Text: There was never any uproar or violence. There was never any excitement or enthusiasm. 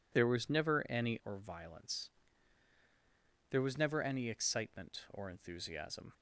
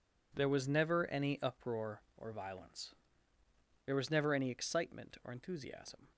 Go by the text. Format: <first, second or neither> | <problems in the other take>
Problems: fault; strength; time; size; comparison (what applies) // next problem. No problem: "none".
second | skips "uproar"; at 1.2 s